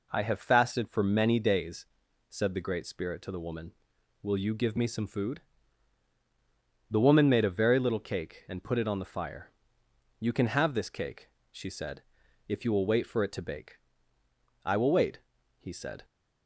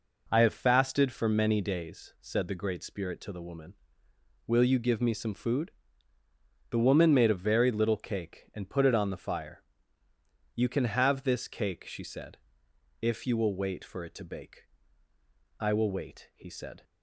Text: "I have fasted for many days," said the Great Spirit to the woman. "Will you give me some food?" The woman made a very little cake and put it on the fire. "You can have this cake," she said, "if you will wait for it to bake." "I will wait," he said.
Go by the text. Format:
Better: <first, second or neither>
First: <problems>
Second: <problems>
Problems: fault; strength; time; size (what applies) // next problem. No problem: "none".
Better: neither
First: none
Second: none